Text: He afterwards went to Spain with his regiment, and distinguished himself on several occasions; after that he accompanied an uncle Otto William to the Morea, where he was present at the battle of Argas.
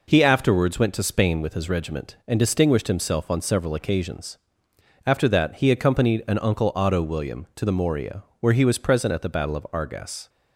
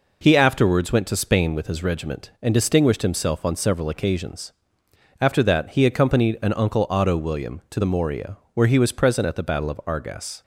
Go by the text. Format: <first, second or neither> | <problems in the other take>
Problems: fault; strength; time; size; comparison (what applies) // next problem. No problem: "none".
neither | none